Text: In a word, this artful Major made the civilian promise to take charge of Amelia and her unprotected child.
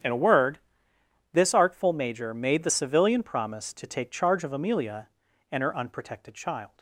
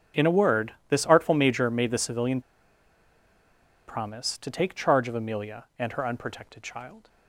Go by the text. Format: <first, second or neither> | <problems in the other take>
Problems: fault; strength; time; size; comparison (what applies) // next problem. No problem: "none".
first | starts louder than the rest; strong; until 1.3 s; 7.5 dB; strong in the first // pauses between "civilian" and "promise"; strong; at 2.3 s; 1.4 s long